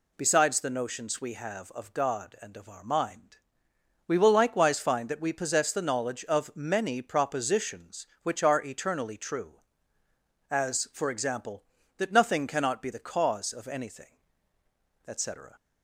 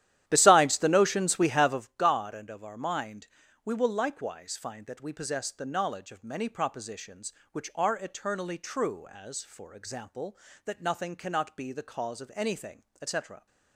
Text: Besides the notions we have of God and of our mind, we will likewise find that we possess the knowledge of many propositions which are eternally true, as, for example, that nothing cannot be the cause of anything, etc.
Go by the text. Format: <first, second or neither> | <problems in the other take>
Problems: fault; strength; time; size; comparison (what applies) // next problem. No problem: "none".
first | starts louder than the rest; strong; until 1.9 s; 12 dB